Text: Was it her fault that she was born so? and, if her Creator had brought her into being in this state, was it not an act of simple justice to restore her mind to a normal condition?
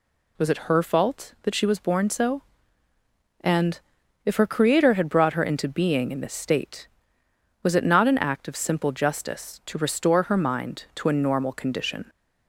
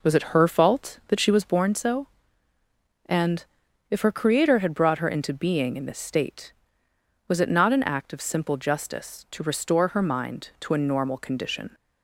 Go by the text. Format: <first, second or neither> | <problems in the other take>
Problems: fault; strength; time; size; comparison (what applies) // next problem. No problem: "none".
first | starts louder than the rest; noticeable; until 1.8 s; 5 dB